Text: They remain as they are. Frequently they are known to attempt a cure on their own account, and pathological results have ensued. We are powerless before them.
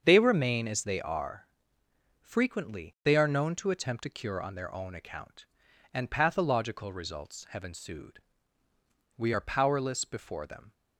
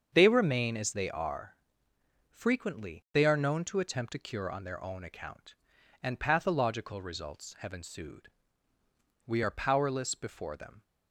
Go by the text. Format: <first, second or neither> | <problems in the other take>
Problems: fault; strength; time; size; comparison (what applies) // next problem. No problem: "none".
neither | starts louder than the rest; the same in both